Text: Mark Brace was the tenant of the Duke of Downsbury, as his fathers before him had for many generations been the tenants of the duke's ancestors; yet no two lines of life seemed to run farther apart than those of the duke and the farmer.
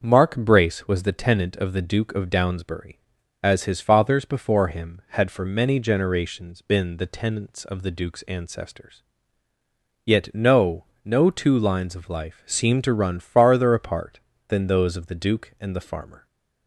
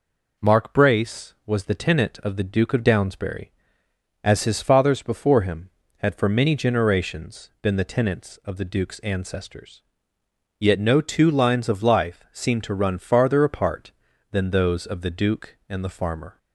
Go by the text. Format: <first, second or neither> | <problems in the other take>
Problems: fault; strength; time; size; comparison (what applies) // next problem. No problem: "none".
second | starts louder than the rest; until 1.0 s; 6.5 dB // says "no" twice; at 11.0 s